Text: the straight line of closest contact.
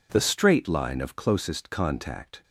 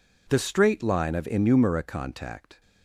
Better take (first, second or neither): first